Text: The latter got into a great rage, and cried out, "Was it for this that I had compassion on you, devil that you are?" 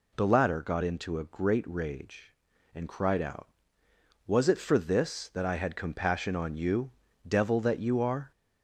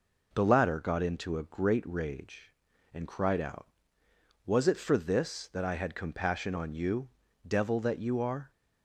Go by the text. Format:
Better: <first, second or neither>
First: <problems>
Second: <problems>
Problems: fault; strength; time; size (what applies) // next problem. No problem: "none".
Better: second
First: gets louder; slight; throughout; 2.5 dB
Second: none